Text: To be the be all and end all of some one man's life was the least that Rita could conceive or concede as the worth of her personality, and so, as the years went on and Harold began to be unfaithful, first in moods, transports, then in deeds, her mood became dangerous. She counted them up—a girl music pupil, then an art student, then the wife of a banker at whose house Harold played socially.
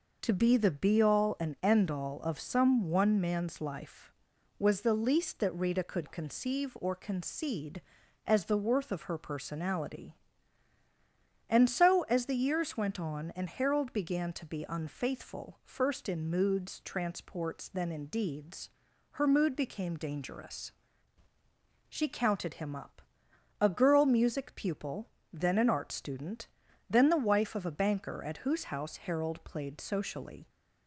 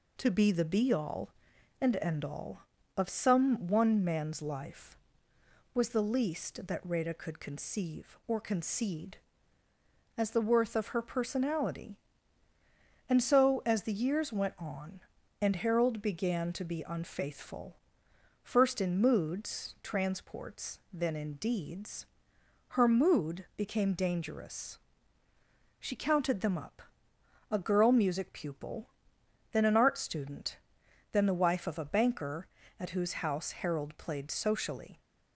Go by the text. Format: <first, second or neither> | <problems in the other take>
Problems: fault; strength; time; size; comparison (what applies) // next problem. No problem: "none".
second | says "him" for "them"; at 22.5 s